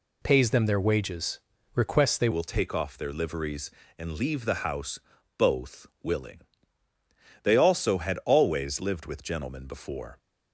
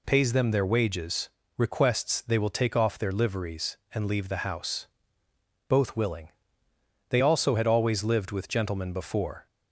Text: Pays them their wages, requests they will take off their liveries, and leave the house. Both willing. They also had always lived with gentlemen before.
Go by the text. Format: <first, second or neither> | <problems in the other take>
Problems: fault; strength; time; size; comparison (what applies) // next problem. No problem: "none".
second | changes voice at "will"; from 2.3 s on; 7.8 s long